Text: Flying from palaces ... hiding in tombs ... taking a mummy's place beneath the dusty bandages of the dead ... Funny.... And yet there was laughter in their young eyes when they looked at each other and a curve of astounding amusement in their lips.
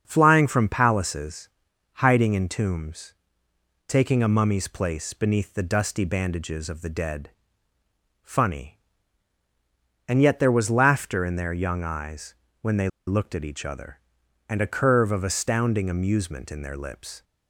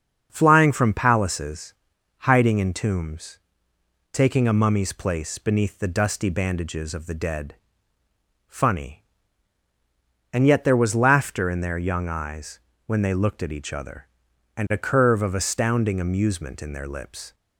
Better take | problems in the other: second | starts louder than the rest; until 1.0 s; 6.5 dB; also in the second // pauses between "eyes" and "when"; slight; at 12.3 s; 0.28 s long; slight in the second // pauses between "they" and "looked"; slight; at 12.8 s; 0.19 s long

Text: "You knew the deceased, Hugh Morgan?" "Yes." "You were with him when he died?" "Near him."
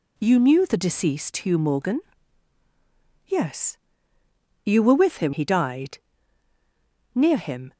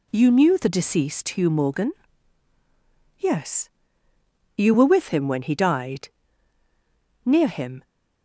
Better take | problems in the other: second | skips "when"; at 5.3 s

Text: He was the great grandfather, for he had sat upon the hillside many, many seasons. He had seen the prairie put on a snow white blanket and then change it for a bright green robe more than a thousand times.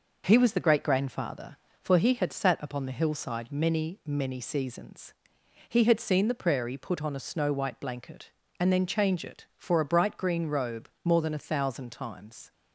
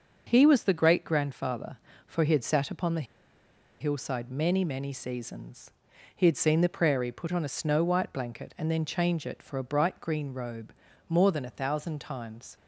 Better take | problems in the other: first | starts louder than the rest; until 1.3 s; 6.5 dB // pauses between "the" and "hillside"; noticeable; at 3.0 s; 0.75 s long // pauses between "robe" and "more"; slight; at 10.7 s; 0.36 s long; slight in the first

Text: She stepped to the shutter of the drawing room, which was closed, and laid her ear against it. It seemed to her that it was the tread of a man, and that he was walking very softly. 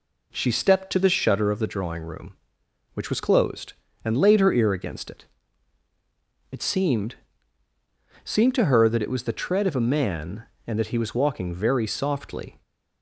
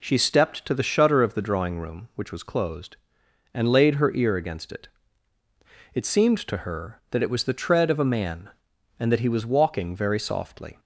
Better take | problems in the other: second | says "seemed" twice; at 8.2 s

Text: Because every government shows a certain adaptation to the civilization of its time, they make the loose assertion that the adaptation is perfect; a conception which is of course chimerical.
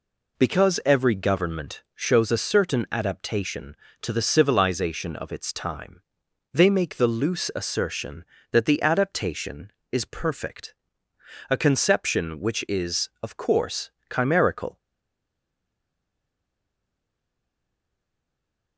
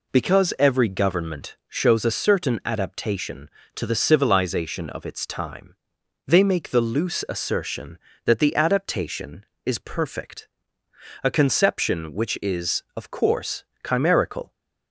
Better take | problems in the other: second | pauses between "course" and "chimerical"; slight; at 13.9 s; 0.18 s long; slight in the second // stays silent after the last word; strong; from 14.7 s on; 4.0 s long

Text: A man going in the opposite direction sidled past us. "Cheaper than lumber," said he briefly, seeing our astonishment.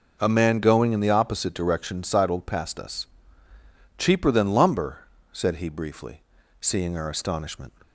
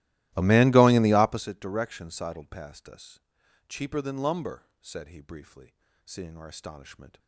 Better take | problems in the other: first | starts louder than the rest; strong; until 1.5 s; 16 dB

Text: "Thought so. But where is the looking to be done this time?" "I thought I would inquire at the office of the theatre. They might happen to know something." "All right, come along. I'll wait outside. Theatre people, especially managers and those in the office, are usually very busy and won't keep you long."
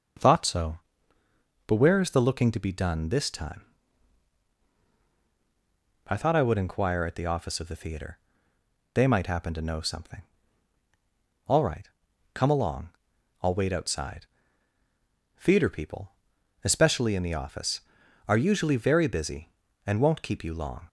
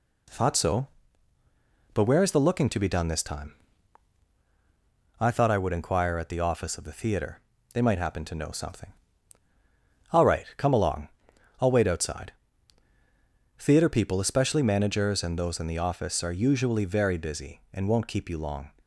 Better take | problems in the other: second | starts louder than the rest; until 2.0 s; 6 dB // skips "managers and those"; at 17.1 s

